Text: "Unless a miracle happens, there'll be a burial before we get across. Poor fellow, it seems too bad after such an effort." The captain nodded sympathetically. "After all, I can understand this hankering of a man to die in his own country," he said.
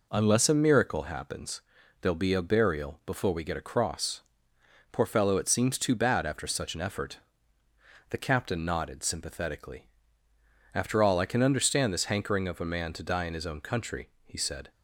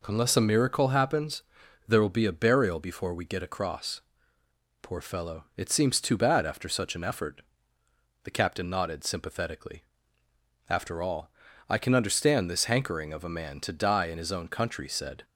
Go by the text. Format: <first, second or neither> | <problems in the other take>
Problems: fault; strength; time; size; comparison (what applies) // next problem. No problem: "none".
first | skips "he"; at 14.8 s